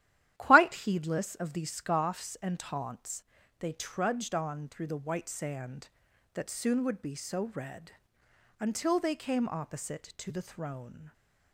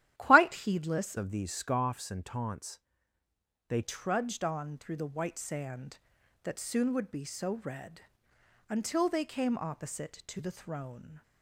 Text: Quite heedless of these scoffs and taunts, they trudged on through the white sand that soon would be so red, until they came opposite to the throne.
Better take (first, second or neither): first